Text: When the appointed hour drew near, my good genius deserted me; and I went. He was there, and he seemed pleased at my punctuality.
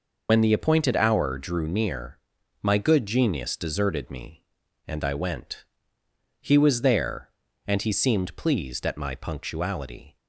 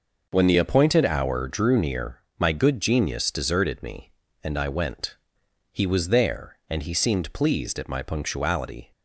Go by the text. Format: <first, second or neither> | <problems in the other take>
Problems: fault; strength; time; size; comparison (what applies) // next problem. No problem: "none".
second | loses the start of "When"; at 0.2 s; 60 ms